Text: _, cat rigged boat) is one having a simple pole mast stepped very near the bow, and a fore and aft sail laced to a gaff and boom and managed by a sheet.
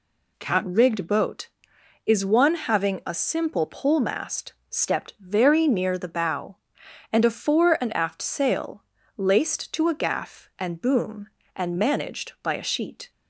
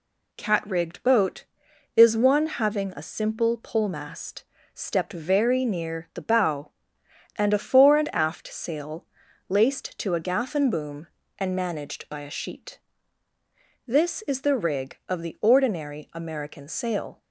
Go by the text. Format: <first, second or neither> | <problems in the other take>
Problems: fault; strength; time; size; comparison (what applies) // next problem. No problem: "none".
first | pauses between "mast" and "stepped"; slight; at 4.4 s; 0.32 s long; slight in the first // pauses between "sail" and "laced"; at 9.0 s; 0.44 s long; slight in the first // goes on to say "This is the rig of the ordinary American sail"; strong; from 13.8 s on; 3.3 s long